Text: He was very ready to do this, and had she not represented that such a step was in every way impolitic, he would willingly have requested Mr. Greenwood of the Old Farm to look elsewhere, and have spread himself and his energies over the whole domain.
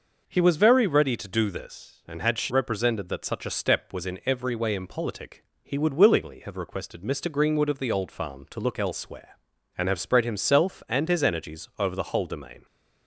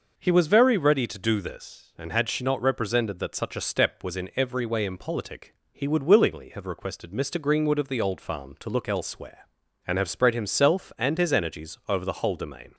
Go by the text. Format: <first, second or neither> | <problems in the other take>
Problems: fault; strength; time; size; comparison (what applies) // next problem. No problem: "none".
second | skips "not"; at 2.5 s